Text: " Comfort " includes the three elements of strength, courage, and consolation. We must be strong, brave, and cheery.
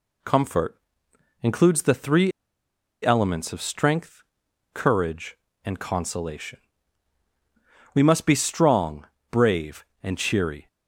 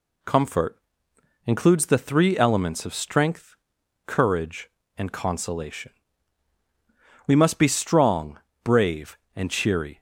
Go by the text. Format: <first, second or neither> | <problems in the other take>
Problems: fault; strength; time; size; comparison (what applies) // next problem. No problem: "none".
second | pauses between "three" and "elements"; noticeable; at 2.3 s; 0.73 s long